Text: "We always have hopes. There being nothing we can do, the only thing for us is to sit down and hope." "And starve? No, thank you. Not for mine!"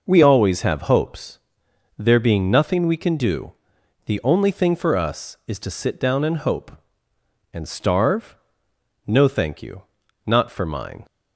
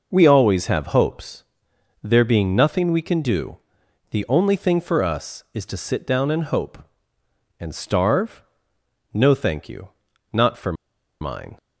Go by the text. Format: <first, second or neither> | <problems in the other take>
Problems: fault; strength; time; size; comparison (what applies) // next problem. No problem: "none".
first | pauses between "for" and "mine"; noticeable; at 10.7 s; 0.47 s long